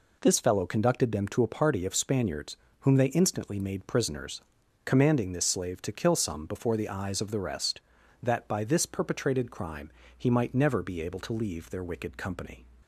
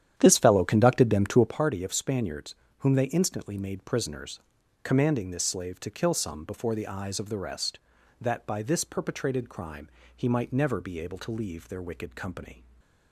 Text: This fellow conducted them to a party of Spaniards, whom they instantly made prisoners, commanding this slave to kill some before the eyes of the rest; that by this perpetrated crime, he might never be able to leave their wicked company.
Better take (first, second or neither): first